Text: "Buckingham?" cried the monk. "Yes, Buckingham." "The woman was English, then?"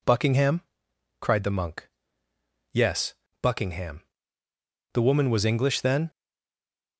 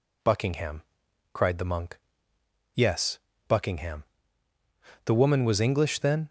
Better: second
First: stays silent after the last word; slight; from 6.0 s on; 0.9 s long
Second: none

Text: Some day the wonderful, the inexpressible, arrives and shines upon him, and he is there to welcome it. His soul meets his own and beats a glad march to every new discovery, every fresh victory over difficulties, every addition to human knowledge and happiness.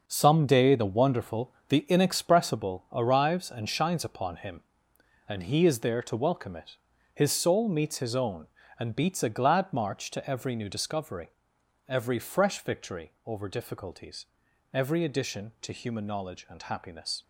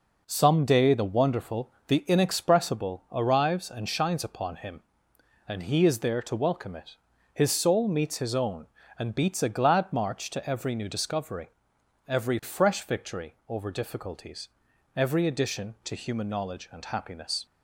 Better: second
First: gets quieter; strong; throughout; 9.5 dB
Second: none

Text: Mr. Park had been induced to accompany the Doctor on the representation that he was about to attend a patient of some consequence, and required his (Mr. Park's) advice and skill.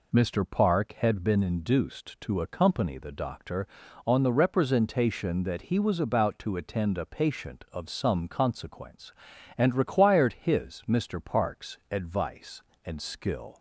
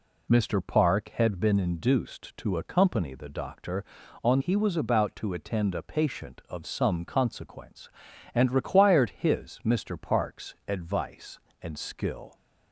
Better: first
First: none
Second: skips "the representation that"; at 4.4 s

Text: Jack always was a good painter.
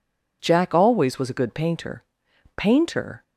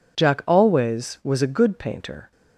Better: second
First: says "painter" twice; at 2.5 s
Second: none

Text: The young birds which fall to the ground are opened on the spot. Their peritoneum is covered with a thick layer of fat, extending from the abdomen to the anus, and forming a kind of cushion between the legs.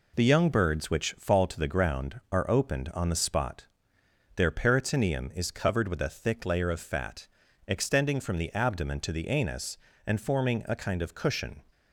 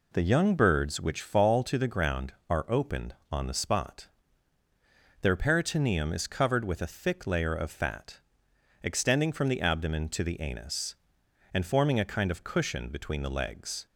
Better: second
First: stops before "between the legs"; at 11.7 s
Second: none

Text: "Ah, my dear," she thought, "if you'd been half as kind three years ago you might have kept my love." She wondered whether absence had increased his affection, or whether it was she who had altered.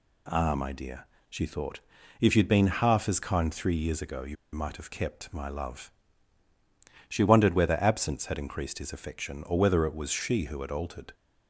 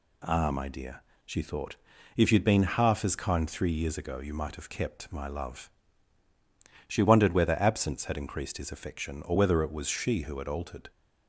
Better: second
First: pauses between "you" and "might"; slight; at 4.3 s; 0.18 s long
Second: none

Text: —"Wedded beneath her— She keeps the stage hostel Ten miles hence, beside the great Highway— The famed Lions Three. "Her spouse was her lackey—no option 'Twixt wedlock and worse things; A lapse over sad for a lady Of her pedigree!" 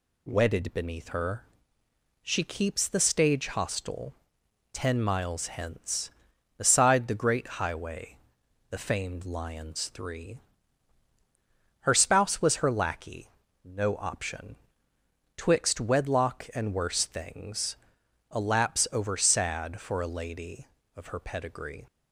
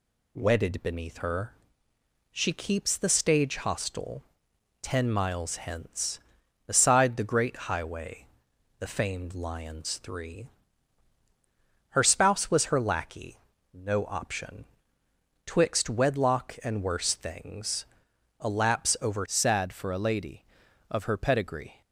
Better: first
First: pauses between "hostel" and "Ten"; noticeable; at 4.1 s; 0.60 s long // pauses between "option" and "Twixt"; noticeable; at 14.5 s; 0.80 s long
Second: pauses between "hostel" and "Ten"; noticeable; at 4.2 s; 0.60 s long // pauses between "option" and "Twixt"; noticeable; at 14.6 s; 0.80 s long // changes voice at "sad"; from 19.2 s on; 2.6 s long

